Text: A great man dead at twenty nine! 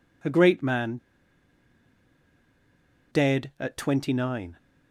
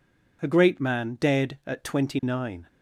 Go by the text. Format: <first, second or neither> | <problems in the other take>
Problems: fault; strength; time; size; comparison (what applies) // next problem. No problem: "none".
second | pauses between "man" and "dead"; strong; at 0.9 s; 2.1 s long